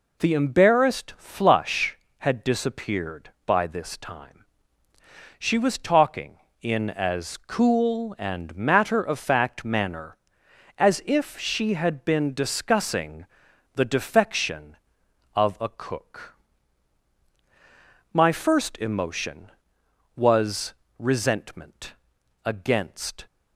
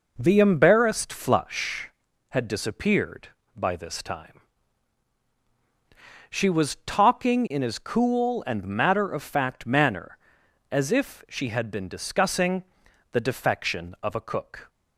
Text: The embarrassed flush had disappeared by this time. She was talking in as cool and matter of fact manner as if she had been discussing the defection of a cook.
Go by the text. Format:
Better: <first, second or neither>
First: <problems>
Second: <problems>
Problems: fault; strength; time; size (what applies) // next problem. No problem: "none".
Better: second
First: pauses between "discussing" and "the"; noticeable; at 13.2 s; 0.48 s long // goes on to say "My first emotion was resentment against"; strong; from 18.1 s on; 5.1 s long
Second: pauses between "discussing" and "the"; noticeable; at 12.6 s; 0.50 s long